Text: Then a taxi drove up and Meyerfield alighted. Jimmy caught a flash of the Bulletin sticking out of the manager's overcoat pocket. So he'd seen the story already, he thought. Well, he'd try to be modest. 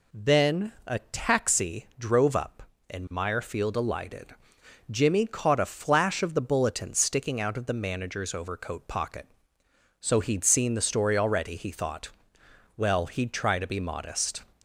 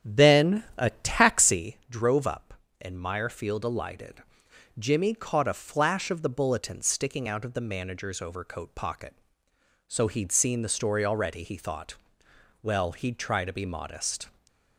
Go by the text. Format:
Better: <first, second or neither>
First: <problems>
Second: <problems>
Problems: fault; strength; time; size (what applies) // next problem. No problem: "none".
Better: first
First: none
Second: starts louder than the rest; strong; until 1.7 s; 8 dB